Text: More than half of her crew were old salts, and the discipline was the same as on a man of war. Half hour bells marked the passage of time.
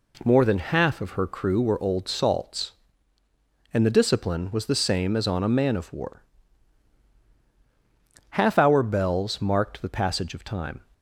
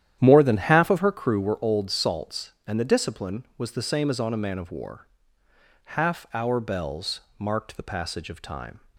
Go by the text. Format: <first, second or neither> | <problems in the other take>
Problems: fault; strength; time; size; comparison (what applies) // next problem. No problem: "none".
first | starts louder than the rest; strong; until 1.2 s; 11 dB // pauses between "bells" and "marked"; slight; at 7.2 s; 0.18 s long